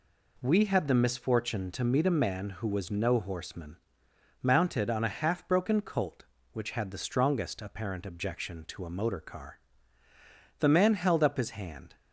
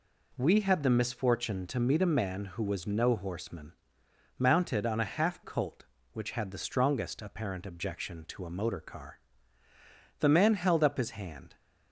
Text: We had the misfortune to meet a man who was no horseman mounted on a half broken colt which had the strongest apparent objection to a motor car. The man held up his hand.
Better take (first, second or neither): first